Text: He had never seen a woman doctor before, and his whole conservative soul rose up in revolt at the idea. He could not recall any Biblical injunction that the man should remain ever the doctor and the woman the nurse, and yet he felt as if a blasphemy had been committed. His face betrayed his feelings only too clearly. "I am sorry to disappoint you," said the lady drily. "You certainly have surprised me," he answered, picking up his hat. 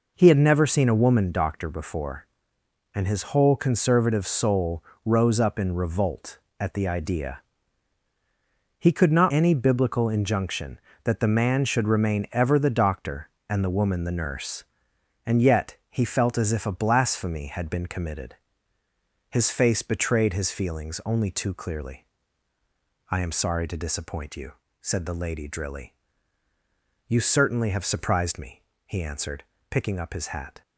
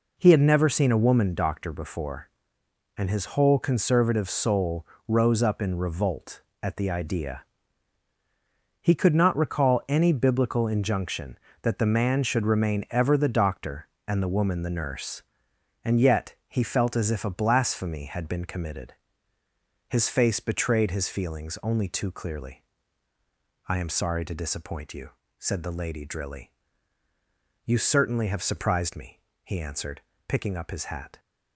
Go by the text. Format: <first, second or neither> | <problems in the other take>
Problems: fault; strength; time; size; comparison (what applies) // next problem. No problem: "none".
second | pauses between "soul" and "rose"; slight; at 4.8 s; 0.22 s long; slight in the second // skips "recall"; at 9.3 s